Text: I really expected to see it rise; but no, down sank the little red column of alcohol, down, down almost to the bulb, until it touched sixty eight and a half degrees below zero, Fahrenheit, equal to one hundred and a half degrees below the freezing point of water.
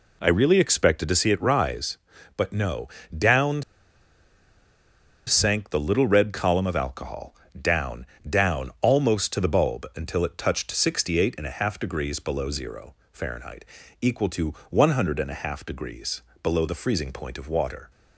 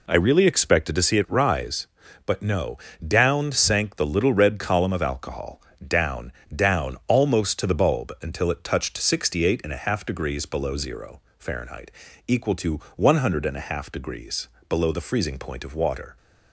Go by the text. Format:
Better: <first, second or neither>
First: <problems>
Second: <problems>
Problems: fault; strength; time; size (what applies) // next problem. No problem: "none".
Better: second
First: pauses between "down" and "sank"; strong; at 3.6 s; 1.6 s long // pauses between "to" and "one"; slight; at 14.5 s; 0.16 s long // pauses between "degrees" and "below"; slight; at 16.2 s; 0.20 s long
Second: pauses between "to" and "one"; slight; at 12.8 s; 0.16 s long // pauses between "degrees" and "below"; slight; at 14.4 s; 0.20 s long